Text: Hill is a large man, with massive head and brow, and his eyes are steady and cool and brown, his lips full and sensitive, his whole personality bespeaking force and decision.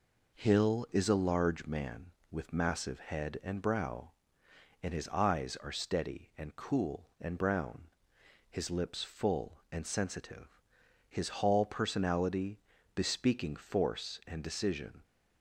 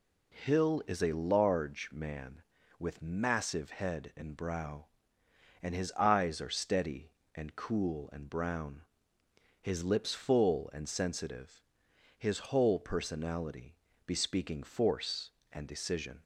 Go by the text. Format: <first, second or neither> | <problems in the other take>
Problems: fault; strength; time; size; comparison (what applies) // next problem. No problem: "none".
second | says "hall" for "whole"; at 11.2 s // pauses between "personality" and "bespeaking"; slight; at 12.5 s; 0.36 s long; slight in the second